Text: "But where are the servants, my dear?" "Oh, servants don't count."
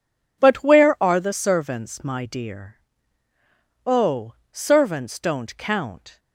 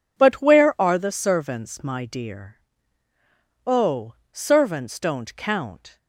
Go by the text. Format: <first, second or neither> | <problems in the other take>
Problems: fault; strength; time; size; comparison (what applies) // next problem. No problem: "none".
neither | none